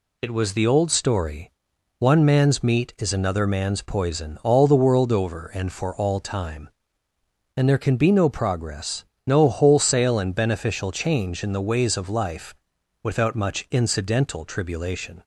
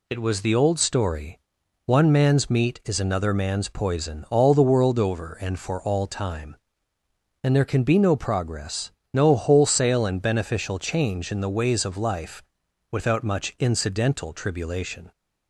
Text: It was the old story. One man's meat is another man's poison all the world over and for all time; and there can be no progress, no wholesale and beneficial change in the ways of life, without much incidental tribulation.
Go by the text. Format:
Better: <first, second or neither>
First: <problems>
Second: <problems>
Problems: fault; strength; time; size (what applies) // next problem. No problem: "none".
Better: neither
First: none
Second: none